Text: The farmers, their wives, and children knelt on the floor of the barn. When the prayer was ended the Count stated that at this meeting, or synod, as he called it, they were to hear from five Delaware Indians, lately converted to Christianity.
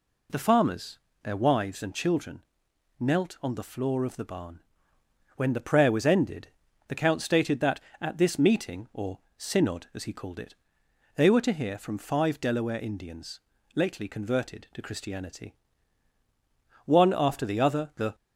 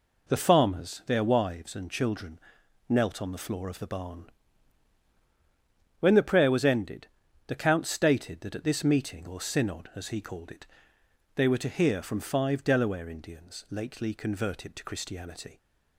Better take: second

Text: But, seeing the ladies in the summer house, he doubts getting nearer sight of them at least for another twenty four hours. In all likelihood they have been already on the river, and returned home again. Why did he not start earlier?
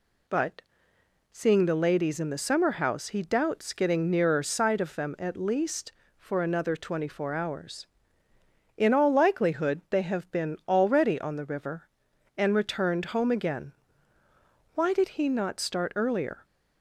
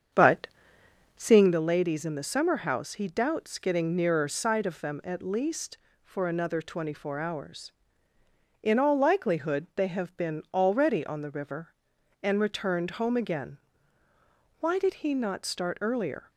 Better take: first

